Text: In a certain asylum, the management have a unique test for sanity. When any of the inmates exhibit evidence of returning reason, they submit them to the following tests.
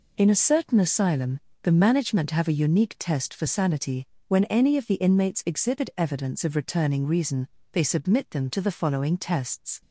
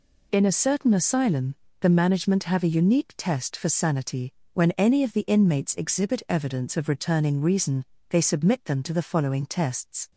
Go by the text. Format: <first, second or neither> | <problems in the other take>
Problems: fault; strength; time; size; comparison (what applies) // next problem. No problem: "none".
neither | none